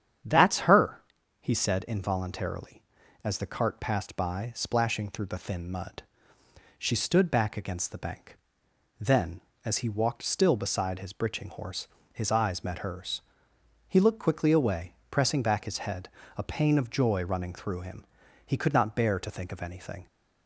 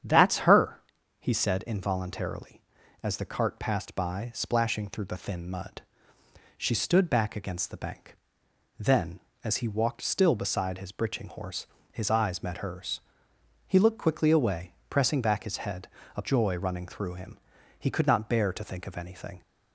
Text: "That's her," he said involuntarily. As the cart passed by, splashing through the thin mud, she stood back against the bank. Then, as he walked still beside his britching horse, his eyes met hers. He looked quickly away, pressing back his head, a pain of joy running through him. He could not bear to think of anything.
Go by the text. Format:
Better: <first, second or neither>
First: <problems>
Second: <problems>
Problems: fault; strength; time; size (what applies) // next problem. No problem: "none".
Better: first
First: starts louder than the rest; strong; until 1.6 s; 8.5 dB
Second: starts louder than the rest; strong; until 1.4 s; 8.5 dB // skips "pain of"; at 16.2 s